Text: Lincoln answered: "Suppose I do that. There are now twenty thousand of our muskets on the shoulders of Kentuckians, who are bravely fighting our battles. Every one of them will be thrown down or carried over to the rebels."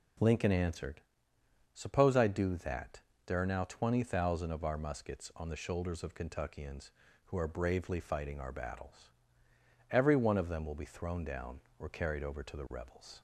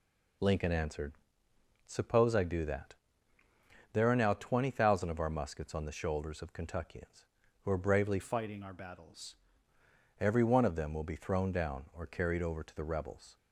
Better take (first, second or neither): first